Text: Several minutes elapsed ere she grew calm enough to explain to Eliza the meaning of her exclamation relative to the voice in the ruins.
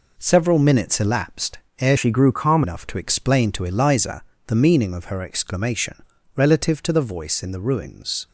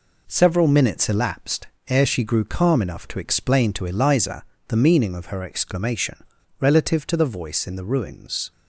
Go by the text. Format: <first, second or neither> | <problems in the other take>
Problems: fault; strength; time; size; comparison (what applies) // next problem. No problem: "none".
second | pauses between "elapsed" and "ere"; slight; at 1.5 s; 0.20 s long; slight in the second // changes voice from "she" to "calm"; from 1.9 to 2.6 s; 0.7 s long // pauses between "Eliza" and "the"; slight; at 4.2 s; 0.24 s long; slight in the second // pauses between "exclamation" and "relative"; slight; at 6.0 s; 0.32 s long; slight in the second